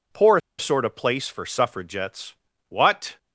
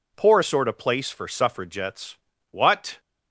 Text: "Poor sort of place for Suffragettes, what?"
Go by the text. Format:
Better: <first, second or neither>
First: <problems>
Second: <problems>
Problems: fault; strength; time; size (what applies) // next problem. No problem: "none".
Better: second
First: pauses between "Poor" and "sort"; slight; at 0.3 s; 0.19 s long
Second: none